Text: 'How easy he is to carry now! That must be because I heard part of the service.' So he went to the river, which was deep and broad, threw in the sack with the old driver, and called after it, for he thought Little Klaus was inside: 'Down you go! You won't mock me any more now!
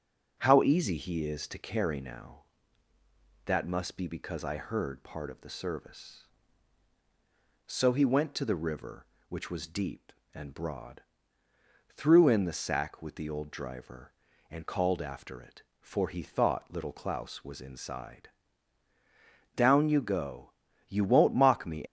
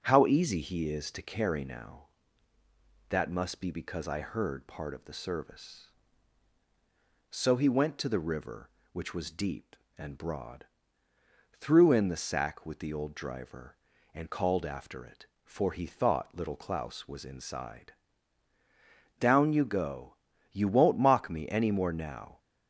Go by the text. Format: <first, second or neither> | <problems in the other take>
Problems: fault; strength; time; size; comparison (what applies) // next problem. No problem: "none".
second | starts louder than the rest; until 1.3 s; 6.5 dB; also in the second // stops before "any more now"; at 21.8 s